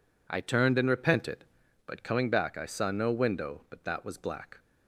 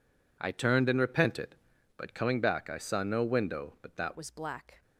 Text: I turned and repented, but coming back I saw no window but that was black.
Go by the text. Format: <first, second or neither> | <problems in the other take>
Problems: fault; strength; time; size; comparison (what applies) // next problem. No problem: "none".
first | changes voice at "was"; from 4.1 s on; 0.7 s long